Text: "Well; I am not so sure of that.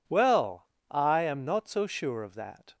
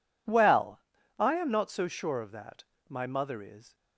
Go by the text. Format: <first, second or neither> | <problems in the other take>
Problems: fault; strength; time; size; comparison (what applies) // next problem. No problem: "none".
first | goes on to say "My mother is"; noticeable; from 2.8 s on; 0.88 s long